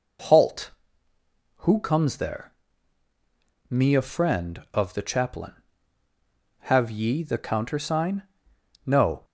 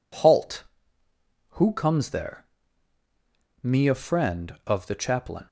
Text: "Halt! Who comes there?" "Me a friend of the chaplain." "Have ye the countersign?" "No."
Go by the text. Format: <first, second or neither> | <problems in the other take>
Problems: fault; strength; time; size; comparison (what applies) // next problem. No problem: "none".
first | stops before "Have ye the countersign No"; at 5.4 s